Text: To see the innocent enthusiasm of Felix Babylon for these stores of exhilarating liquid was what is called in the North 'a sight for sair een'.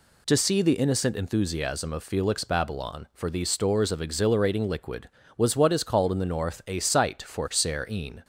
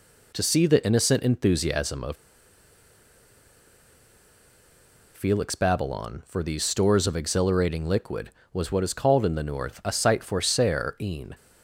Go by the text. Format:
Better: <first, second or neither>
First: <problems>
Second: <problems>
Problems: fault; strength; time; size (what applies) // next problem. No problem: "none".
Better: first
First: none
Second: pauses between "of" and "Felix"; strong; at 2.1 s; 2.9 s long